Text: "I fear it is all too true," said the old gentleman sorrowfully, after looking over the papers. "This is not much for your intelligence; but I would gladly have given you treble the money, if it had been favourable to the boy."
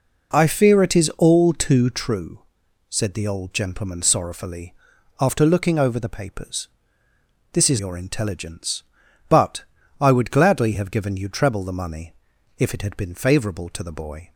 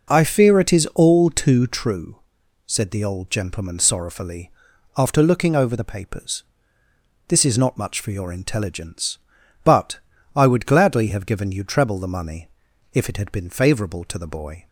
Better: second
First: skips "not much for"; at 7.7 s // pauses between "but" and "I"; slight; at 9.6 s; 0.34 s long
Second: pauses between "but" and "I"; slight; at 9.9 s; 0.34 s long

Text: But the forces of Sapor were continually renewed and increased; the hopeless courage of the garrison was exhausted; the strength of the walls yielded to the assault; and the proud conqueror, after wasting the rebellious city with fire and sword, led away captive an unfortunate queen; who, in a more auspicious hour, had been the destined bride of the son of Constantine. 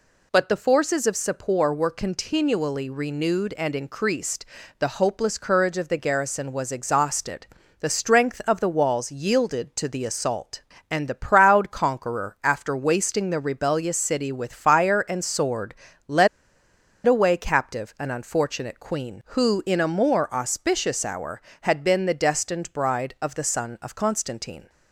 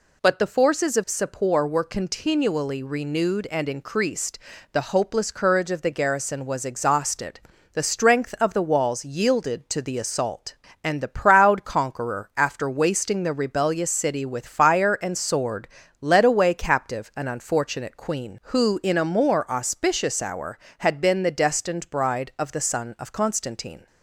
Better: second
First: pauses between "led" and "away"; noticeable; at 16.2 s; 0.79 s long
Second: none

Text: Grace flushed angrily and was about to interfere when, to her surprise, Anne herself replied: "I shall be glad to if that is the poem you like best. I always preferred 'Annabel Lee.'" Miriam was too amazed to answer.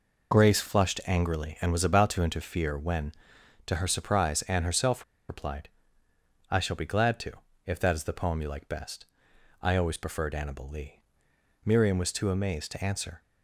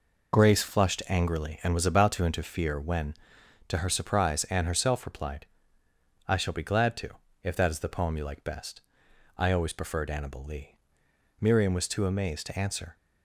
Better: second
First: pauses between "herself" and "replied"; slight; at 5.0 s; 0.24 s long // pauses between "to" and "if"; slight; at 7.3 s; 0.34 s long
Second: pauses between "to" and "if"; slight; at 7.1 s; 0.34 s long

